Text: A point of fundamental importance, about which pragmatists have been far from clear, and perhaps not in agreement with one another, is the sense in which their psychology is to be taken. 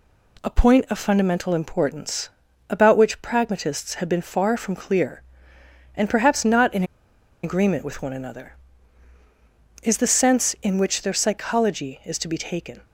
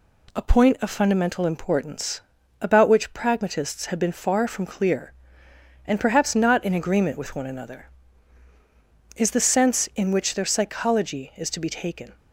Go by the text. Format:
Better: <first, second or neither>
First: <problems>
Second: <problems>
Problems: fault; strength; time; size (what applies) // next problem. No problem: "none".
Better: second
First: pauses between "in" and "agreement"; noticeable; at 6.8 s; 0.59 s long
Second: none